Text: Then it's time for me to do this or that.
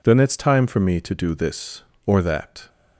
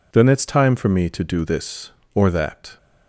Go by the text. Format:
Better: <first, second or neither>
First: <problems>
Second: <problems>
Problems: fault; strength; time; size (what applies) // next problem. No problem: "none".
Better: neither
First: none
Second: none